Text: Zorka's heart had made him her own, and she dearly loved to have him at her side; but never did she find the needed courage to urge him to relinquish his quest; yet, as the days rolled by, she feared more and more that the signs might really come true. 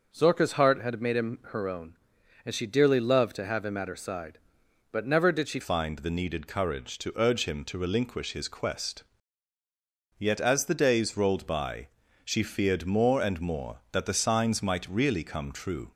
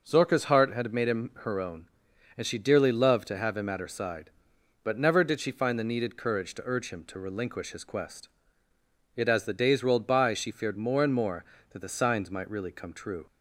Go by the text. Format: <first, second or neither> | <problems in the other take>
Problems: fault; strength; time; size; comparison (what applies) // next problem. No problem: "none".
second | changes voice at "find"; from 5.6 s on; 10.3 s long